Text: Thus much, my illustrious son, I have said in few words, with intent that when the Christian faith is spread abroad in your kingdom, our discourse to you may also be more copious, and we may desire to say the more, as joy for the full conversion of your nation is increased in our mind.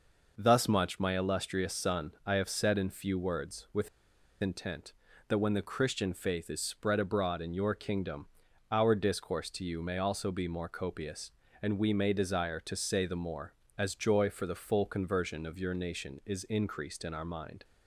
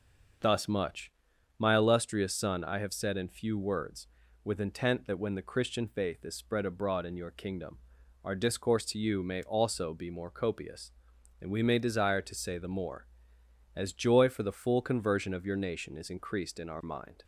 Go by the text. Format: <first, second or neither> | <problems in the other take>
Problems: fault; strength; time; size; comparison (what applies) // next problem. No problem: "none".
second | pauses between "with" and "intent"; noticeable; at 3.8 s; 0.52 s long